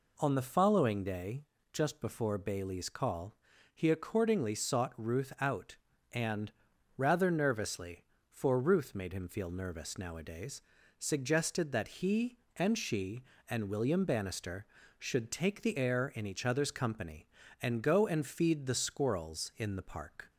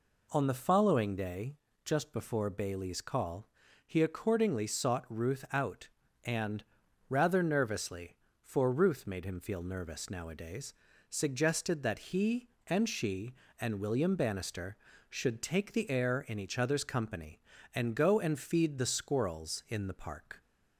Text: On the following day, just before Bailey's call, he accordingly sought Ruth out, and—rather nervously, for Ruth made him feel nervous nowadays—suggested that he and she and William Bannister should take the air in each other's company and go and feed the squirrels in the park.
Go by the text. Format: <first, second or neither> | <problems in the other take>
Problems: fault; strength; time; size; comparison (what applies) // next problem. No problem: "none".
neither | none